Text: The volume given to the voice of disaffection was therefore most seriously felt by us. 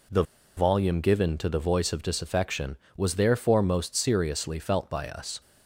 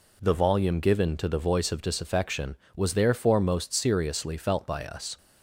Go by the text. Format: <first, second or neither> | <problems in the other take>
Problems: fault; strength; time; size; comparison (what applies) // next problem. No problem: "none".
second | pauses between "The" and "volume"; slight; at 0.2 s; 0.34 s long